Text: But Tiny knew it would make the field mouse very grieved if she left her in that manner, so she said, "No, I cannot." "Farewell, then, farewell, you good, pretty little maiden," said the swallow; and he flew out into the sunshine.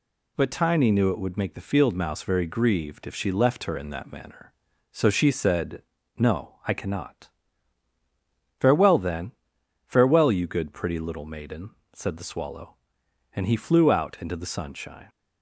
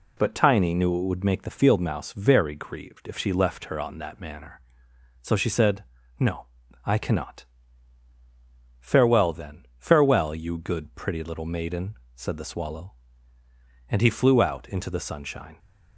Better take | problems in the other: first | says "on" for "in"; at 3.8 s

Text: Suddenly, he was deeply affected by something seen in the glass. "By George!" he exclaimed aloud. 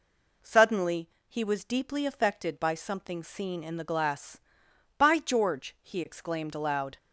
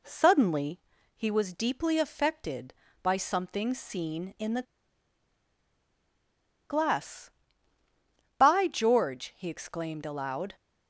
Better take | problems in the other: first | pauses between "the" and "glass"; strong; at 4.6 s; 2.0 s long

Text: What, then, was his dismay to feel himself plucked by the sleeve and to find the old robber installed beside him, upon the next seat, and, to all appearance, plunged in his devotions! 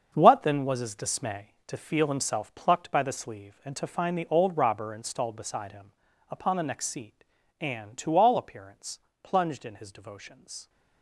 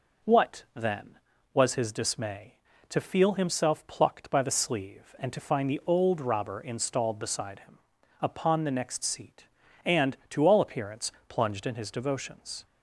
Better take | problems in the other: second | gets quieter; strong; throughout; 11 dB

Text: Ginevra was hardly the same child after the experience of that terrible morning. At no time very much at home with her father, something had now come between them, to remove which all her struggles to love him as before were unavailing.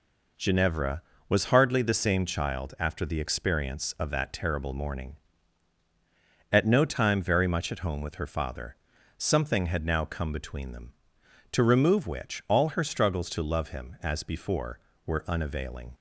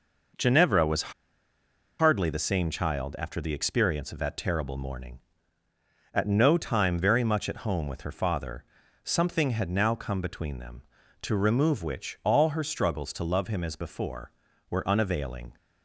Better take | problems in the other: first | pauses between "was" and "hardly"; noticeable; at 1.1 s; 0.87 s long

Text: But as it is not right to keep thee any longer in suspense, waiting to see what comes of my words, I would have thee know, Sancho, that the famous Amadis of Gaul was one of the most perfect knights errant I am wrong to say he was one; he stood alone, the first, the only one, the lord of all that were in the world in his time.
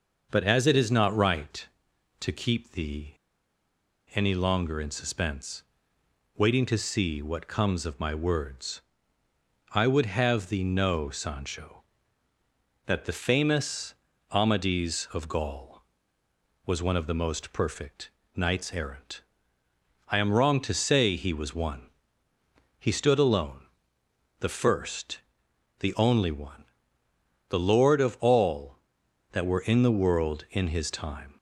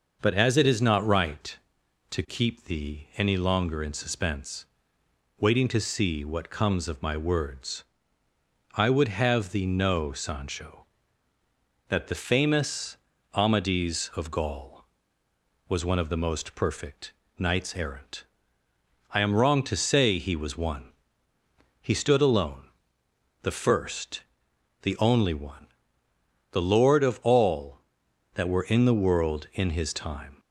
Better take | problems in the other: second | starts louder than the rest; noticeable; until 1.3 s; 6 dB; noticeable in the second // pauses between "thee" and "any"; at 3.1 s; 1.0 s long // pauses between "famous" and "Amadis"; at 13.9 s; 0.38 s long; also in the second // pauses between "perfect" and "knights"; slight; at 18.1 s; 0.26 s long; slight in the second // pauses between "errant" and "I"; noticeable; at 19.2 s; 0.90 s long; noticeable in the second

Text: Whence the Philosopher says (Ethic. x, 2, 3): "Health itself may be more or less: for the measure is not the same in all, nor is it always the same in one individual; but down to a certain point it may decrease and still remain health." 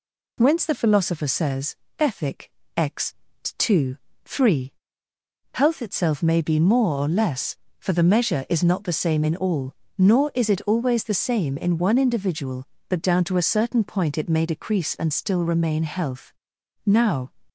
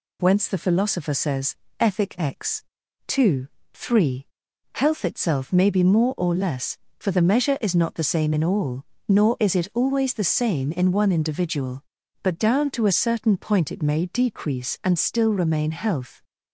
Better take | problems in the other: second | goes on to say "Now"; slight; from 16.8 s on; 0.46 s long

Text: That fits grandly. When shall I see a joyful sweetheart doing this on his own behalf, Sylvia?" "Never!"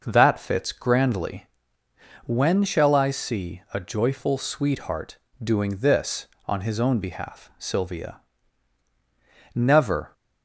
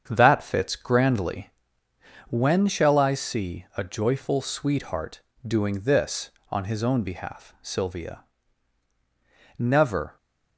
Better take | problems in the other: first | gets quieter; throughout; 6.5 dB // pauses between "sweetheart" and "doing"; slight; at 5.2 s; 0.24 s long; slight in the first

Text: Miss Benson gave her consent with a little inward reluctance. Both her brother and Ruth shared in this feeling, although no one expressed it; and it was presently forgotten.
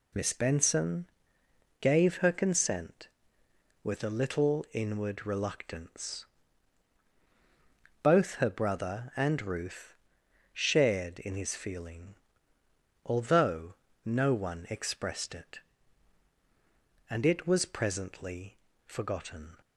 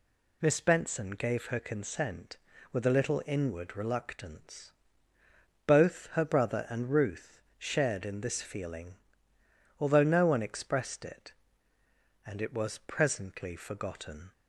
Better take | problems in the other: second | pauses between "Benson" and "gave"; noticeable; at 1.0 s; 0.74 s long // pauses between "Ruth" and "shared"; noticeable; at 9.9 s; 0.58 s long; slight in the second // says "his" for "this"; at 11.3 s // pauses between "although" and "no"; slight; at 13.7 s; 0.30 s long // pauses between "presently" and "forgotten"; slight; at 18.5 s; 0.26 s long

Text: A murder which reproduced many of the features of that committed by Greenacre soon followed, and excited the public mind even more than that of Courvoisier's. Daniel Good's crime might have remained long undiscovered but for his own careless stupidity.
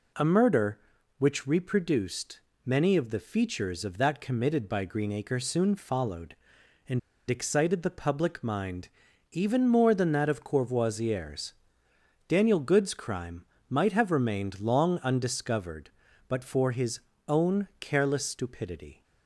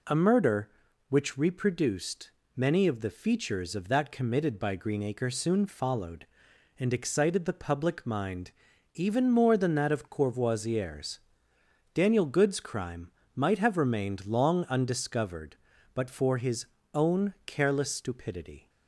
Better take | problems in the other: second | pauses between "reproduced" and "many"; slight; at 2.3 s; 0.28 s long; slight in the second // pauses between "and" and "excited"; slight; at 6.9 s; 0.29 s long // pauses between "mind" and "even"; at 8.8 s; 0.42 s long; also in the second // pauses between "crime" and "might"; slight; at 13.4 s; 0.24 s long; slight in the second // pauses between "his" and "own"; slight; at 17.0 s; 0.26 s long; slight in the second

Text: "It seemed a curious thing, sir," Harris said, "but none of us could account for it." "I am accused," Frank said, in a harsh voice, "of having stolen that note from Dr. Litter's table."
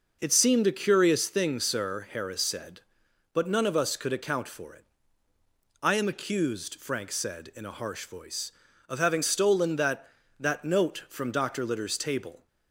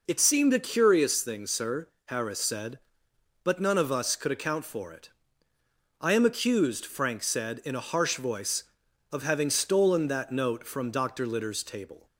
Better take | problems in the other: second | says "that" twice; at 10.3 s

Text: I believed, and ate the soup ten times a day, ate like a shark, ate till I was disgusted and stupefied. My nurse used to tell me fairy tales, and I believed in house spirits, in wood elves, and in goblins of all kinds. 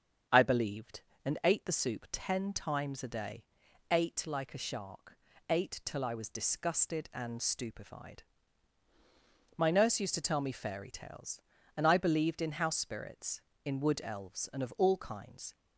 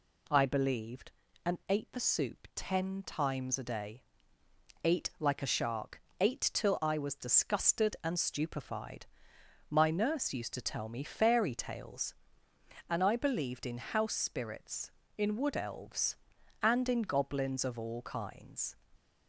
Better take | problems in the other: second | starts louder than the rest; strong; until 1.5 s; 7.5 dB // skips "in goblins"; at 14.6 s

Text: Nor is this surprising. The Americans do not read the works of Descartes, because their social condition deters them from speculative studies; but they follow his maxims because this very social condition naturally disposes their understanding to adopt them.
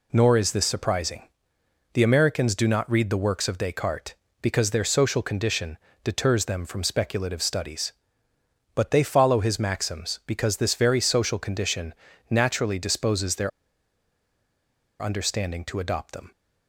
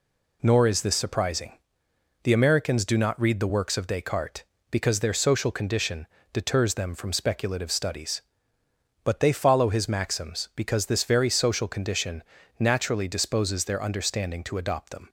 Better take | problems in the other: second | pauses between "condition" and "deters"; slight; at 5.7 s; 0.26 s long; slight in the second // pauses between "condition" and "naturally"; at 11.9 s; 0.38 s long; also in the second // pauses between "their" and "understanding"; strong; at 13.5 s; 1.5 s long

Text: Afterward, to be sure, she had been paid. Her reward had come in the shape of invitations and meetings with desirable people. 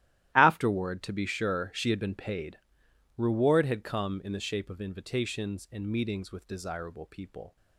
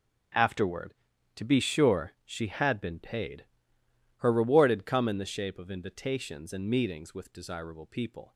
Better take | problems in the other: second | starts louder than the rest; strong; until 1.3 s; 14 dB // skips "Her"; at 2.8 s

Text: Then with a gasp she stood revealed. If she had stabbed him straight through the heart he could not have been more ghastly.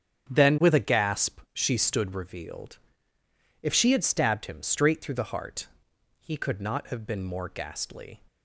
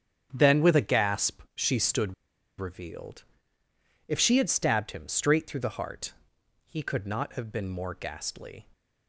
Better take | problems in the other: first | starts louder than the rest; strong; until 1.3 s; 9 dB; strong in the first // pauses between "stood" and "revealed"; at 2.1 s; 0.45 s long // pauses between "heart" and "he"; noticeable; at 6.1 s; 0.52 s long; noticeable in the first

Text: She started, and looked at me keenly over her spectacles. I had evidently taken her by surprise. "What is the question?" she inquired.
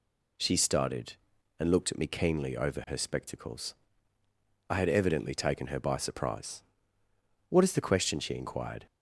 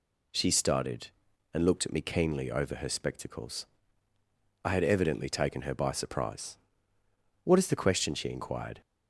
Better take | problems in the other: neither | none

